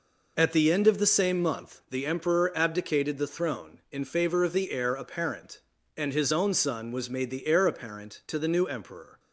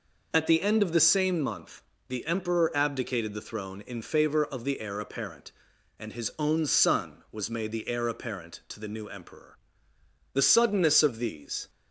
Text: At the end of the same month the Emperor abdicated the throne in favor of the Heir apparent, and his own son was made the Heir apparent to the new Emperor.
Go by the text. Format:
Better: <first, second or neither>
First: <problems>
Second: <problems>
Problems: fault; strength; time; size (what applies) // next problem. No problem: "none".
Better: first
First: none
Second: pauses between "month" and "the"; slight; at 1.8 s; 0.26 s long // goes on to say "The suddenness of these"; from 10.3 s on; 1.3 s long